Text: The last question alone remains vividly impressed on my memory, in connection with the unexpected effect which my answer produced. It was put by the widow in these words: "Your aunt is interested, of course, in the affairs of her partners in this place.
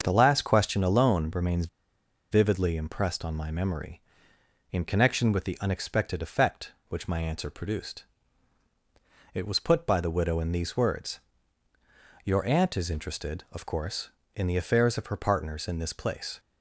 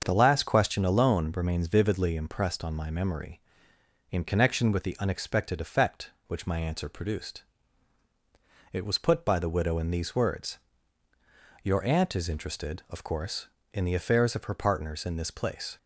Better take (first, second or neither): second